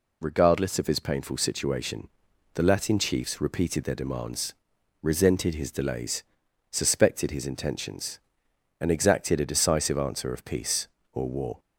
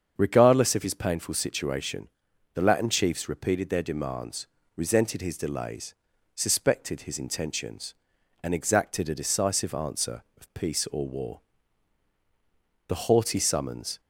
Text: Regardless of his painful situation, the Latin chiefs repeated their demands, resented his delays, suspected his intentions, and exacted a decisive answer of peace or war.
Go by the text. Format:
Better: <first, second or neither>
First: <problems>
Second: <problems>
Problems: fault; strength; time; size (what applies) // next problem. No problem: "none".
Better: first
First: none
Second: starts louder than the rest; strong; until 1.1 s; 7 dB // goes on to say "The haughty summons"; noticeable; from 12.8 s on; 1.1 s long